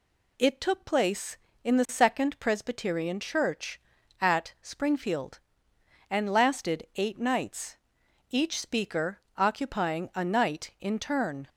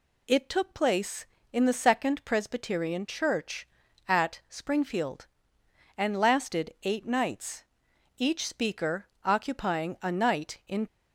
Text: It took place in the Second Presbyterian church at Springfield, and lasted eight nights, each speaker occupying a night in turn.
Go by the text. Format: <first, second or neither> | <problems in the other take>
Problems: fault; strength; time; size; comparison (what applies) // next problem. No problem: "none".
first | pauses between "speaker" and "occupying"; slight; at 9.0 s; 0.18 s long; slight in the first // stops before "turn"; at 10.8 s